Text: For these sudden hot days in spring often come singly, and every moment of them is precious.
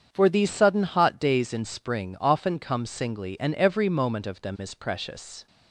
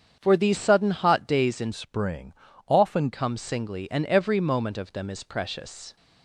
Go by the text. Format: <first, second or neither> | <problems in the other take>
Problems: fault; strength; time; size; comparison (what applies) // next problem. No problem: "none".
first | starts louder than the rest; strong; until 1.2 s; 7.5 dB; strong in the first // changes voice from "spring" to "often"; from 1.7 to 3.1 s; 1.4 s long // pauses between "spring" and "often"; slight; at 2.3 s; 0.32 s long